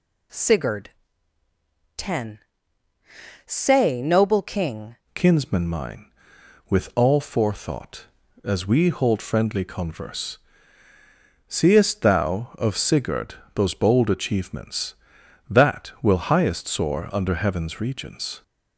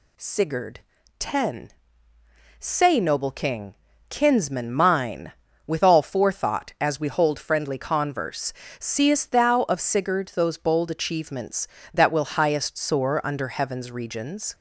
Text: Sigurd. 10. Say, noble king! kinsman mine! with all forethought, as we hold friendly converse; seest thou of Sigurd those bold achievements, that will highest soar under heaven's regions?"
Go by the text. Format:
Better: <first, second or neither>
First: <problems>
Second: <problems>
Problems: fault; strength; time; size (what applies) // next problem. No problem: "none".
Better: second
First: changes voice at "kinsman"; from 5.1 s on; 13.3 s long // pauses between "Sigurd" and "those"; slight; at 13.3 s; 0.20 s long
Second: none